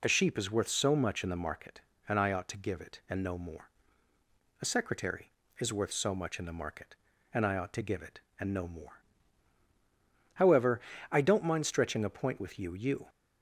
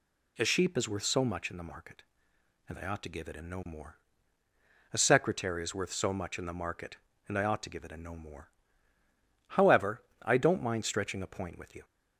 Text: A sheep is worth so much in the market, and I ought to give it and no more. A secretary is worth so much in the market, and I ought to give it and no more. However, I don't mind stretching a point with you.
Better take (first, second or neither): second